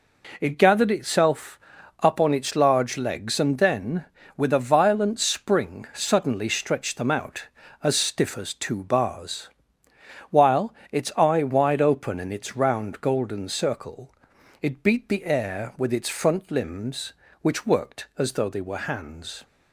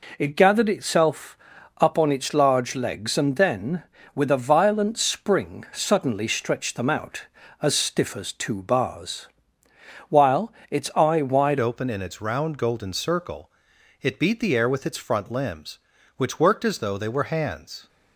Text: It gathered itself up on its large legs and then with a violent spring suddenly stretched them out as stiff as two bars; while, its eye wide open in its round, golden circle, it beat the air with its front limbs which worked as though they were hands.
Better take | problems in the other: first | pauses between "itself" and "up"; at 1.3 s; 0.40 s long; also in the first // changes voice at "open"; from 11.5 s on; 6.3 s long

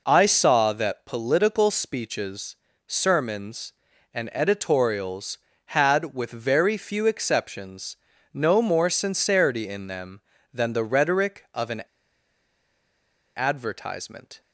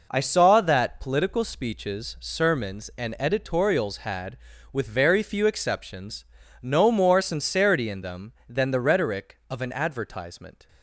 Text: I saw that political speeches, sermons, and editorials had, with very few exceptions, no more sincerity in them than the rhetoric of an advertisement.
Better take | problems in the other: second | pauses between "an" and "advertisement"; strong; at 11.8 s; 1.5 s long

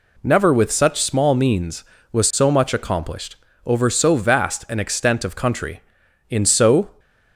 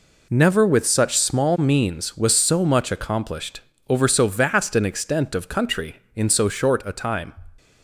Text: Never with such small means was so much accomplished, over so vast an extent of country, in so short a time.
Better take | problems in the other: second | stops before "short a time"; at 6.9 s

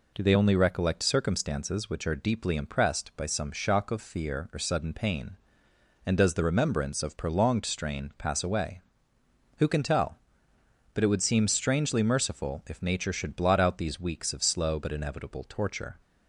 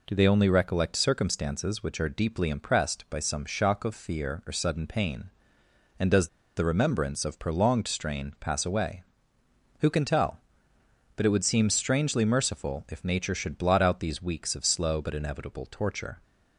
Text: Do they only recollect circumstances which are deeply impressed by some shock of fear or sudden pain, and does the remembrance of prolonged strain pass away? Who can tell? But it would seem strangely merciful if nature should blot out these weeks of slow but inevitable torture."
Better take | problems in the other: first | pauses between "does" and "the"; slight; at 6.2 s; 0.29 s long

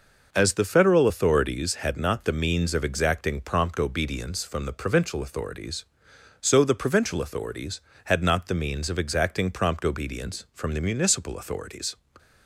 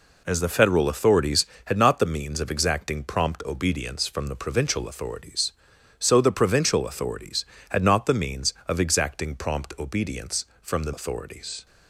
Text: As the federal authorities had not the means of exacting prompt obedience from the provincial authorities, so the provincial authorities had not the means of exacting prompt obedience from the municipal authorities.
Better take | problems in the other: first | skips "municipal"; at 10.9 s

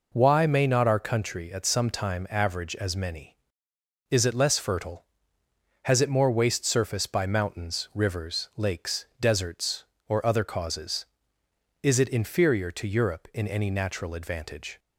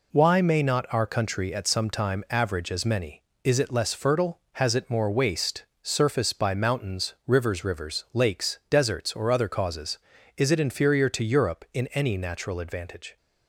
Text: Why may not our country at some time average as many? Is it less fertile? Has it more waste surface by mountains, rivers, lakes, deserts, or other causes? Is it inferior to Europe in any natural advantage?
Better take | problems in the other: first | pauses between "waste" and "surface"; slight; at 5.6 s; 0.18 s long // says "rivers" twice; at 7.6 s

